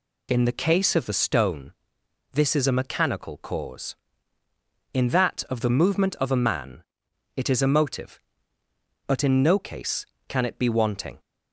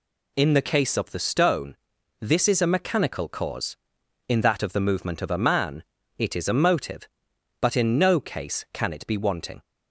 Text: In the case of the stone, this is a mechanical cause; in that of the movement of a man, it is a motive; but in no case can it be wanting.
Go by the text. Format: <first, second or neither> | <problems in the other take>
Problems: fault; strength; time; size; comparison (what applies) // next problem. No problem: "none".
neither | none